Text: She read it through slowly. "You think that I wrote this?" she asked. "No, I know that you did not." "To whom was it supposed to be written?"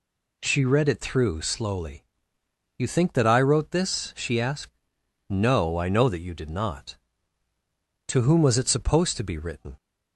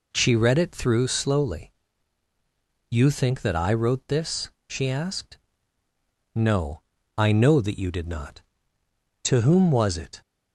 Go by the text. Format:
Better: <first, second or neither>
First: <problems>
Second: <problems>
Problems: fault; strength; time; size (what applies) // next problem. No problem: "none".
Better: first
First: none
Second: stops before "supposed to be written"; at 10.2 s